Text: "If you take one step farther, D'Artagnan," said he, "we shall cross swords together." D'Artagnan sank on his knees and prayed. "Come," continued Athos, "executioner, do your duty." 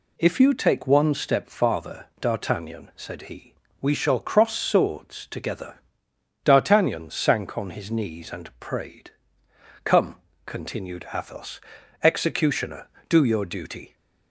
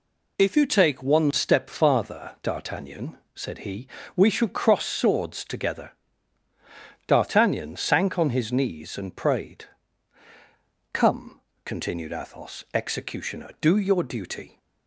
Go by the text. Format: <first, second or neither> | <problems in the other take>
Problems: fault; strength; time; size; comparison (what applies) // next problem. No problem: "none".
neither | none